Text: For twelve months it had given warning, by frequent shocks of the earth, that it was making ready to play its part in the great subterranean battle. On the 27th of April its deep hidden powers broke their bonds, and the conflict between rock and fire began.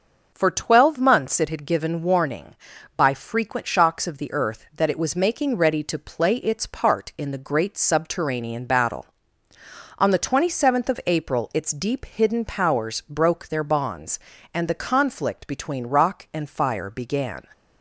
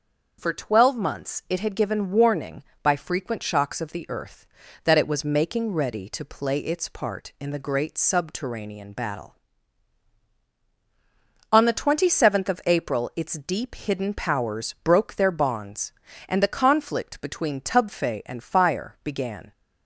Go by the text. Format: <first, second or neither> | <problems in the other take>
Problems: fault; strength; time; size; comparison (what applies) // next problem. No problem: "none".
first | starts louder than the rest; until 1.4 s; 6 dB // says "tubfe" for "rock"; at 17.5 s